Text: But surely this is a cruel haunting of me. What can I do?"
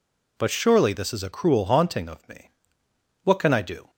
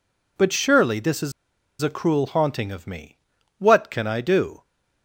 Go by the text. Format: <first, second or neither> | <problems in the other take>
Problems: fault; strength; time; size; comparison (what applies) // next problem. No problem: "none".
first | pauses between "is" and "a"; noticeable; at 1.3 s; 0.50 s long